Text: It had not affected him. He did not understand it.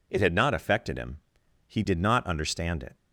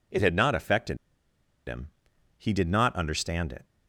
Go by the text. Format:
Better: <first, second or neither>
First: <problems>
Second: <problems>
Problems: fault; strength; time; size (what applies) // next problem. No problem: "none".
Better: first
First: none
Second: pauses between "affected" and "him"; noticeable; at 0.9 s; 0.71 s long